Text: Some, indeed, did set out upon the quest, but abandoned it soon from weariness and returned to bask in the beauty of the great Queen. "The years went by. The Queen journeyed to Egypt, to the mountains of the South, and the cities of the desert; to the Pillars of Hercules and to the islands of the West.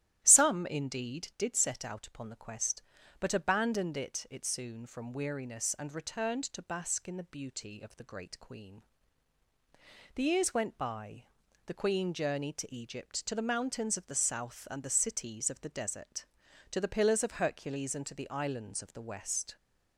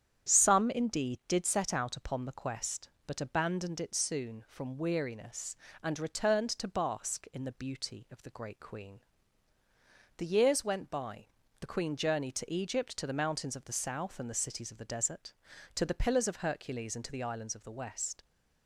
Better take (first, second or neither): second